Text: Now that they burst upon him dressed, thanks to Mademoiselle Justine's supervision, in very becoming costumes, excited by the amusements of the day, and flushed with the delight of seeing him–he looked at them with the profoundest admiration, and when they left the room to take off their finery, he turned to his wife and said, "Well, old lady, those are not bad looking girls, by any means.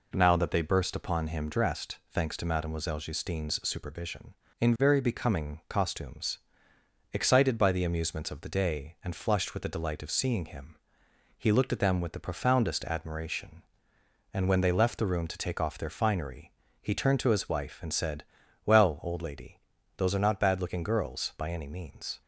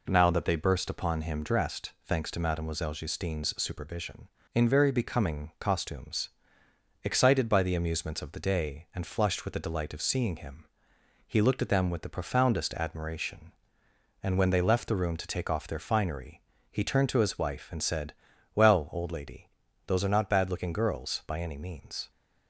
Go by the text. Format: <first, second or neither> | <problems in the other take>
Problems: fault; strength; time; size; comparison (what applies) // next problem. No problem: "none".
neither | none